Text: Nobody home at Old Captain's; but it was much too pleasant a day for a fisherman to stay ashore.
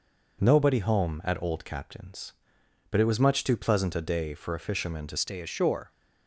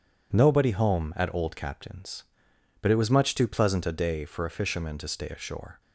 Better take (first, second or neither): second